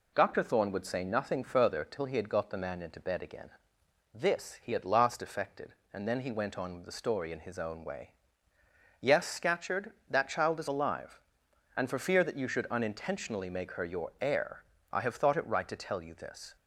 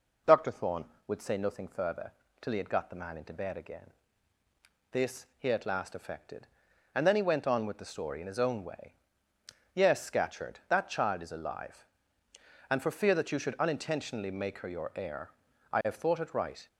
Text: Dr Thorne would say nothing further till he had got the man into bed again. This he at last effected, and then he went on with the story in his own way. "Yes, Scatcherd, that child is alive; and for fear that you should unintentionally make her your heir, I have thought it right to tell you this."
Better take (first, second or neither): first